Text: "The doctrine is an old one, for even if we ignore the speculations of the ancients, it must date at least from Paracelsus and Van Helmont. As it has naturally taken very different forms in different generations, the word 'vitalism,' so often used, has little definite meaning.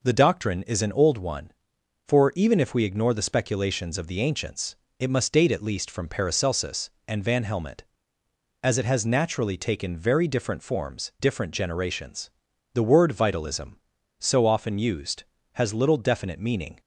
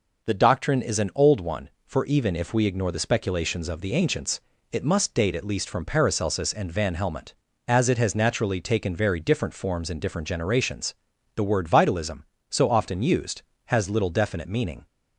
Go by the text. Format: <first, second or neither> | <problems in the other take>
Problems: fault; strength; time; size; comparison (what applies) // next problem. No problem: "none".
second | skips "in"; at 11.1 s